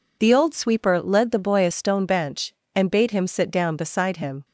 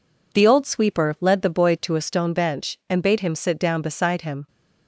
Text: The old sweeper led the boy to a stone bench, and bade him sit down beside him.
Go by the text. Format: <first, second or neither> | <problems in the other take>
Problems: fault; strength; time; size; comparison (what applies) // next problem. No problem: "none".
second | skips "to"; at 1.6 s